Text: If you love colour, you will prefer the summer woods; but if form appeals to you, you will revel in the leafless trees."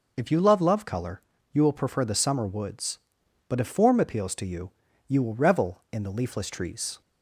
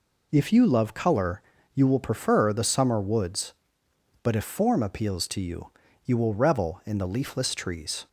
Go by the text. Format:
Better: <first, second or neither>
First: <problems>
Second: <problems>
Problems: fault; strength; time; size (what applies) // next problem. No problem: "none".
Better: second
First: says "love" twice; at 0.6 s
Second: none